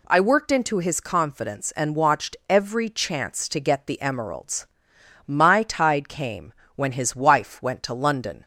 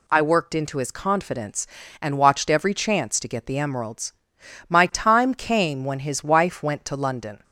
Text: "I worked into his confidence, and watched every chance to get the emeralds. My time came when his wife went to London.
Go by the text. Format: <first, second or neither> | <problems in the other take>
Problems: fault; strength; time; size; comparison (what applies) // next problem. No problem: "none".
second | says "tide" for "time"; at 5.6 s // pauses between "came" and "when"; slight; at 6.5 s; 0.24 s long